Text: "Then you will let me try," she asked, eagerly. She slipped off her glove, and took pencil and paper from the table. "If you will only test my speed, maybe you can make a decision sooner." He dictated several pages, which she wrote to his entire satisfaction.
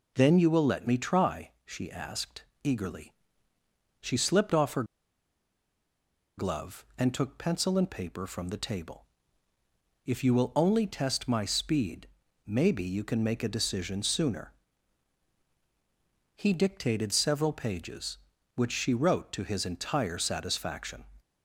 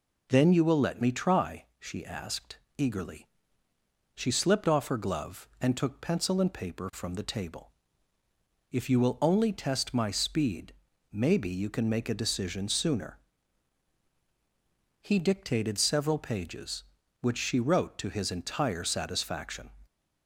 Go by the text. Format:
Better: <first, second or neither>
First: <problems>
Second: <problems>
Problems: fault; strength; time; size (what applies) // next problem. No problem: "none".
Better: second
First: pauses between "her" and "glove"; strong; at 4.8 s; 1.5 s long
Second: none